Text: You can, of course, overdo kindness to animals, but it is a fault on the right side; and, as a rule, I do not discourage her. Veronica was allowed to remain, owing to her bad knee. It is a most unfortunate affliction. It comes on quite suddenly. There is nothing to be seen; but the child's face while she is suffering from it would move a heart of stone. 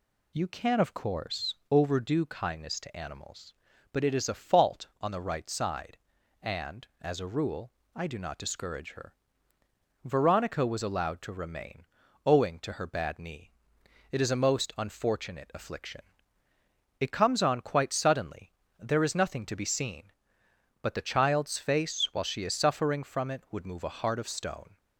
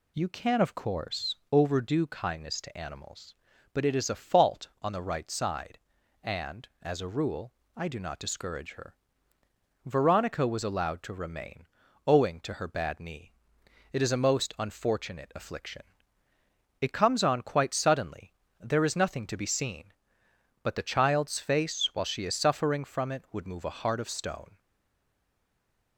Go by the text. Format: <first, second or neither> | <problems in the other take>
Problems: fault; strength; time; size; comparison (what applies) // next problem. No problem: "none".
first | stays silent after the last word; noticeable; from 24.5 s on; 1.4 s long